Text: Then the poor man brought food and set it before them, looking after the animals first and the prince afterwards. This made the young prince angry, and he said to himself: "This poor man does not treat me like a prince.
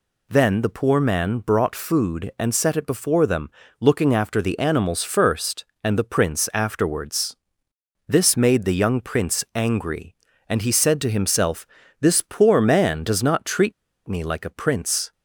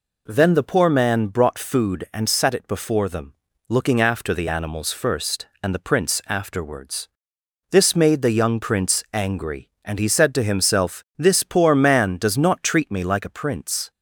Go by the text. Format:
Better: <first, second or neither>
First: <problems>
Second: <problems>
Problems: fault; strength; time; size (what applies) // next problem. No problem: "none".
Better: second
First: pauses between "treat" and "me"; slight; at 13.7 s; 0.34 s long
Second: none